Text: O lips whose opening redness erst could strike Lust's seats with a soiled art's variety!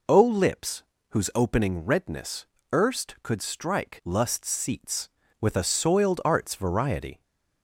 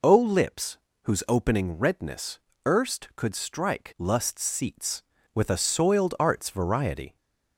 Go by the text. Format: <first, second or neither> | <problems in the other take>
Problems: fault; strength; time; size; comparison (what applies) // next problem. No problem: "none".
neither | pauses between "lips" and "whose"; slight; the same in both // pauses between "redness" and "erst"; slight; the same in both